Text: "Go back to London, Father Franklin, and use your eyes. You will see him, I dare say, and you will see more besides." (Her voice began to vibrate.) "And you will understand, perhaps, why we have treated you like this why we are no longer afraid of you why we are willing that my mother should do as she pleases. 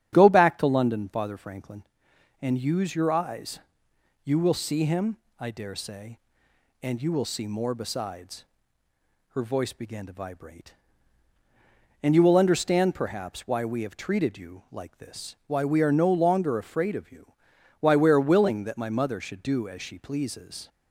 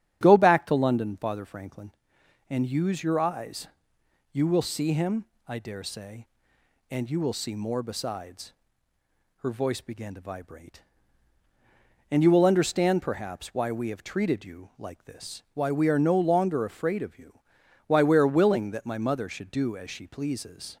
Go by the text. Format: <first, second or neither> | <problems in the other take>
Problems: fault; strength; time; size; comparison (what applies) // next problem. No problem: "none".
neither | starts louder than the rest; strong; the same in both // pauses between "you" and "why"; noticeable; the same in both